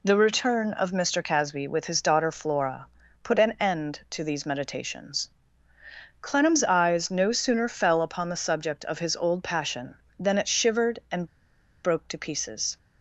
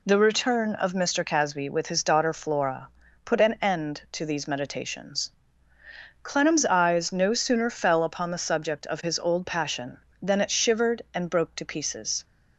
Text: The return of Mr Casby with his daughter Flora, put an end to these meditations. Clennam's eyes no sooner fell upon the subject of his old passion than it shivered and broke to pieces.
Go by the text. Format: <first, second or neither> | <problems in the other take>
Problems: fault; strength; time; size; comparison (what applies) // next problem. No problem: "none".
second | pauses between "and" and "broke"; noticeable; at 11.2 s; 0.57 s long